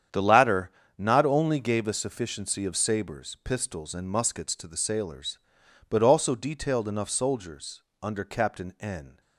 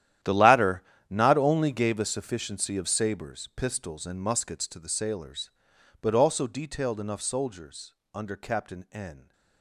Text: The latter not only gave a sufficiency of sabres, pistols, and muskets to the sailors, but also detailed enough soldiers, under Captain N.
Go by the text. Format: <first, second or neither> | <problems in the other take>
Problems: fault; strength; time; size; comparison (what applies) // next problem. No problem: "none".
first | gets quieter; strong; throughout; 17 dB // starts louder than the rest; strong; until 1.5 s; 11.5 dB; strong in the first // pauses between "latter" and "not"; slight; at 0.8 s; 0.26 s long; slight in the first